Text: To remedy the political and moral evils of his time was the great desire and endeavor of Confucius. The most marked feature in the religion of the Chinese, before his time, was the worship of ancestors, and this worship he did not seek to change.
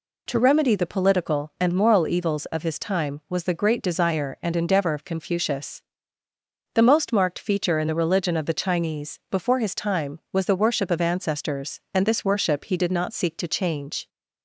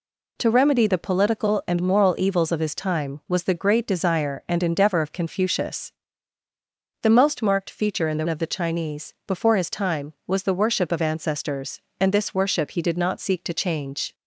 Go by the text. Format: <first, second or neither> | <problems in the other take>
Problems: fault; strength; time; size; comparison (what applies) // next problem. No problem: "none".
first | skips "religion"; at 8.2 s